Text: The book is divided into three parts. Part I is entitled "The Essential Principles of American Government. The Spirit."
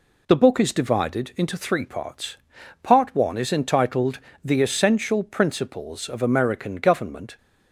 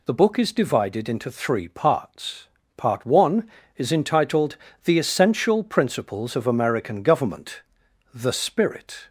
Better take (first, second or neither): second